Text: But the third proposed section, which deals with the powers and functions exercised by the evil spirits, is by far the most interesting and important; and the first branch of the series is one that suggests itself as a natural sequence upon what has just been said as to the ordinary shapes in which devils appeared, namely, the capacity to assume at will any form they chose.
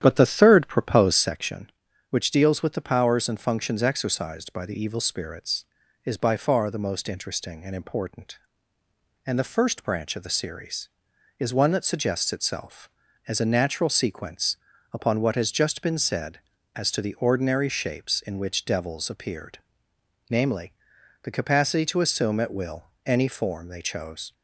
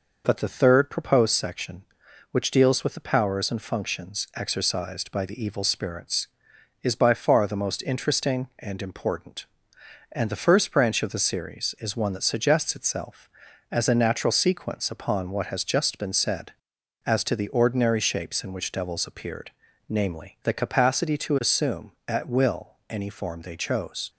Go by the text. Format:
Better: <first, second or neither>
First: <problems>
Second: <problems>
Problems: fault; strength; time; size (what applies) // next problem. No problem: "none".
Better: second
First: starts louder than the rest; strong; until 1.4 s; 10 dB // pauses between "sequence" and "upon"; slight; at 14.5 s; 0.36 s long // pauses between "will" and "any"; slight; at 22.8 s; 0.20 s long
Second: pauses between "will" and "any"; slight; at 22.7 s; 0.16 s long